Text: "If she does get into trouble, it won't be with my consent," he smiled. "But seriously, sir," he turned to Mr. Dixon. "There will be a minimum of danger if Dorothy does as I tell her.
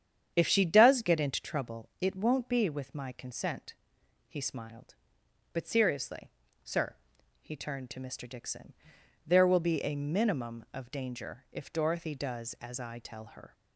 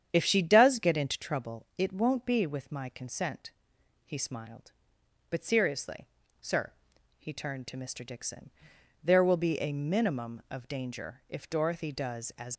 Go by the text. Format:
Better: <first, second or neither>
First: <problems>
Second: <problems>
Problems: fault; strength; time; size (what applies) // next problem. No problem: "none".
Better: first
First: starts louder than the rest; strong; until 1.3 s; 8.5 dB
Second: starts louder than the rest; strong; until 1.1 s; 8.5 dB // stops before "I tell her"; at 12.5 s